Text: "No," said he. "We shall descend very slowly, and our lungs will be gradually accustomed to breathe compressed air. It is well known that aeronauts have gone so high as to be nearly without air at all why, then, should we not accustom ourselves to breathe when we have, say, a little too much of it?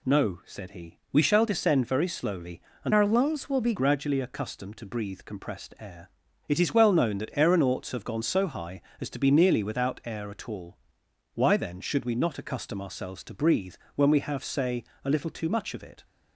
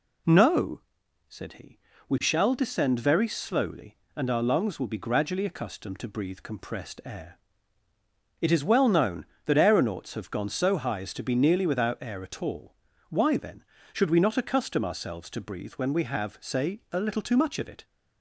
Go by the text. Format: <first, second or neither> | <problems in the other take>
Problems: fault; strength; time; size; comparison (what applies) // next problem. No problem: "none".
second | changes voice from "our" to "be"; from 2.9 to 3.7 s; 0.8 s long // pauses between "all" and "why"; noticeable; at 10.7 s; 0.58 s long; slight in the second // pauses between "breathe" and "when"; slight; at 13.7 s; 0.18 s long